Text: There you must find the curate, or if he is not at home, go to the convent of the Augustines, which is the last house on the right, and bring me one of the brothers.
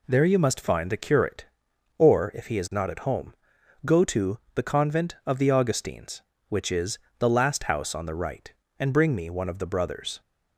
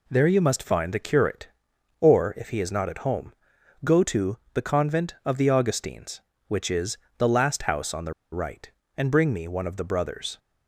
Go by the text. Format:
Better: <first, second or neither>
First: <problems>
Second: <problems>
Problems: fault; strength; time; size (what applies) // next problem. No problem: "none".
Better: first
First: pauses between "to" and "the"; slight; at 4.3 s; 0.16 s long // pauses between "is" and "the"; slight; at 6.9 s; 0.20 s long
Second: pauses between "to" and "the"; slight; at 4.3 s; 0.16 s long // pauses between "is" and "the"; slight; at 6.9 s; 0.20 s long // pauses between "the" and "right"; slight; at 8.1 s; 0.19 s long